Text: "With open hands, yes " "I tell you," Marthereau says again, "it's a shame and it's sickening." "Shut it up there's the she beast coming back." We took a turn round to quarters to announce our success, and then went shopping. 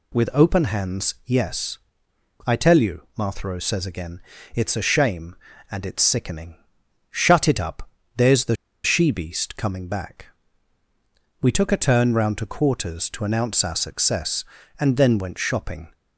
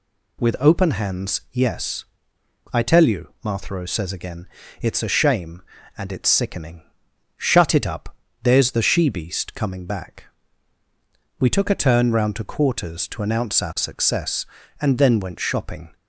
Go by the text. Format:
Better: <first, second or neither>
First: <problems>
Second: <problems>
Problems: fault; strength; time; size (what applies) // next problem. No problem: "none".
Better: second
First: pauses between "up" and "there's"; slight; at 7.8 s; 0.26 s long // pauses between "the" and "she"; slight; at 8.5 s; 0.29 s long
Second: pauses between "up" and "there's"; slight; at 8.1 s; 0.26 s long